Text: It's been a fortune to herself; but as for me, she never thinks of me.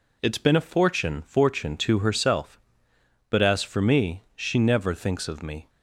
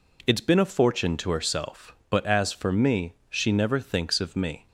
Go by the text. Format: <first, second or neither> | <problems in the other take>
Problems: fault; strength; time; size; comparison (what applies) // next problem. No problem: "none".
second | says "fortune" twice; at 1.2 s